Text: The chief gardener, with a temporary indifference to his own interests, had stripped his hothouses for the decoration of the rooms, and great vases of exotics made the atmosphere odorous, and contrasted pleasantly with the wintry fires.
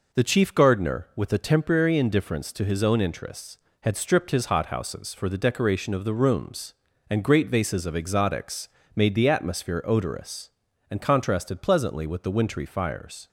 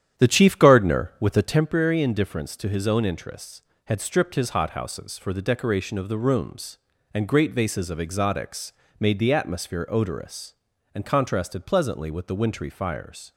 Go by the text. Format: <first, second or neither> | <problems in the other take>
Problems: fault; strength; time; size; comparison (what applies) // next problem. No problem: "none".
first | starts louder than the rest; strong; until 1.6 s; 10 dB // pauses between "exotics" and "made"; slight; at 8.7 s; 0.26 s long; slight in the first